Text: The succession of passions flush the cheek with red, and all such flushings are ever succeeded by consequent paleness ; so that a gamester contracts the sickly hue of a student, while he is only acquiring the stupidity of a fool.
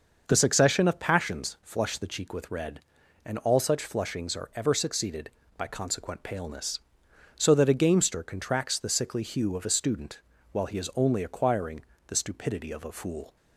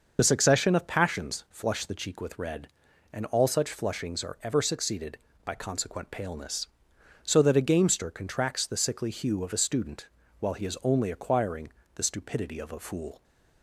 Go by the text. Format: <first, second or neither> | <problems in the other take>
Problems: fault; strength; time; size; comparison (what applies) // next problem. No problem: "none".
first | loses the start of "The"; at 0.1 s; 40 ms // starts louder than the rest; until 1.1 s; 6 dB; also in the first // pauses between "acquiring" and "the"; slight; at 11.7 s; 0.24 s long; slight in the first